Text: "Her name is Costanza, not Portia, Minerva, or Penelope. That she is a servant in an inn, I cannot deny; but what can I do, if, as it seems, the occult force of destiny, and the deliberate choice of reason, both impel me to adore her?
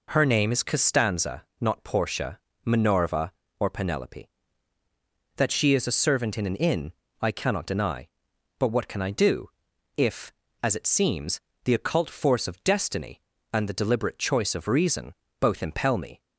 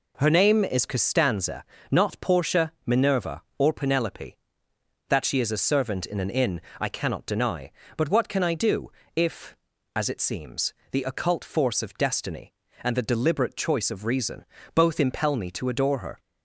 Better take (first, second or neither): second